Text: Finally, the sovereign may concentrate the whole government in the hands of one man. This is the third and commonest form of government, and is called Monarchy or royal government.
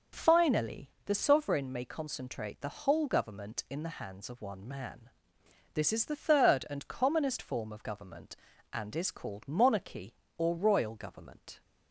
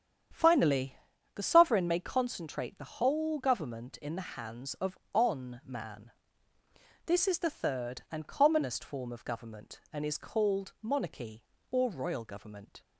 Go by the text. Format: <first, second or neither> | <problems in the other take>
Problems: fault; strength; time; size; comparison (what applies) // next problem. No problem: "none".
first | starts louder than the rest; strong; until 1.6 s; 8.5 dB; also in the first // says "on" for "one"; at 5.1 s